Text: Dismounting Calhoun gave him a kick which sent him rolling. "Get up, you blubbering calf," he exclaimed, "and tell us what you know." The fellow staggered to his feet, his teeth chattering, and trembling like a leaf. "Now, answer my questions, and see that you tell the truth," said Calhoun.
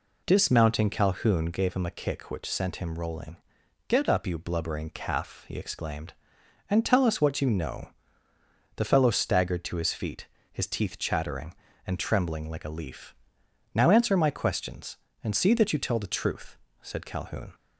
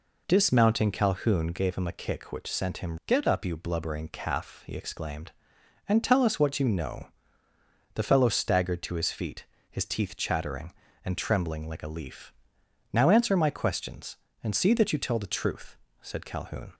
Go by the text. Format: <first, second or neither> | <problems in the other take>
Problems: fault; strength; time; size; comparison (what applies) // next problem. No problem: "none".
first | skips "rolling"; at 3.0 s